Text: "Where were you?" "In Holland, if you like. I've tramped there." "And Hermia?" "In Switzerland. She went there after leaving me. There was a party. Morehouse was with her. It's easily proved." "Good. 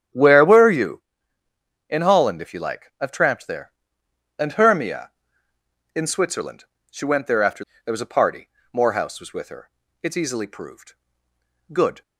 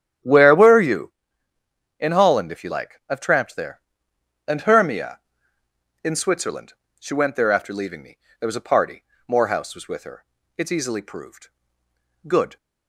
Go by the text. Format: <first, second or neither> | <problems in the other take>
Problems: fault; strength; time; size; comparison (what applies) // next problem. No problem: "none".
second | starts louder than the rest; strong; until 1.9 s; 9.5 dB; strong in the second // skips "leaving me"; at 7.7 s